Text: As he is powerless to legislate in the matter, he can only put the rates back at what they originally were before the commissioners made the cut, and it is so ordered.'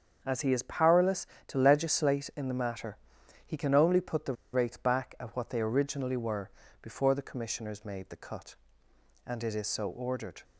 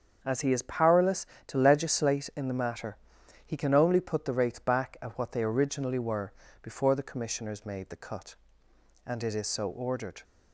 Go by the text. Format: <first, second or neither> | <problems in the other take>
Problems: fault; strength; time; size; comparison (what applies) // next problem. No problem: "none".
second | starts louder than the rest; until 1.2 s; 7 dB; also in the second // pauses between "the" and "rates"; slight; at 4.3 s; 0.19 s long // pauses between "were" and "before"; slight; at 6.4 s; 0.32 s long; slight in the second